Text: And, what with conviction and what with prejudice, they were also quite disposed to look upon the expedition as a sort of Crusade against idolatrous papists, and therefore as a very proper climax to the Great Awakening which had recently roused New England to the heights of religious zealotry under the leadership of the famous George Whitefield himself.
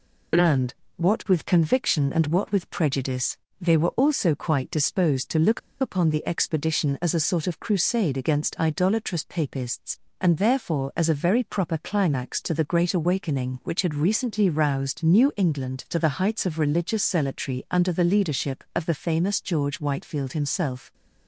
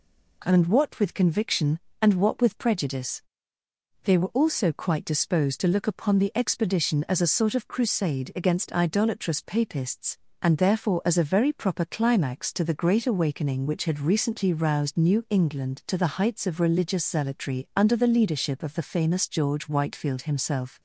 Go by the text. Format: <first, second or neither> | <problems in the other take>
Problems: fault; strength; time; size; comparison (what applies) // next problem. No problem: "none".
second | pauses between "look" and "upon"; slight; at 5.5 s; 0.21 s long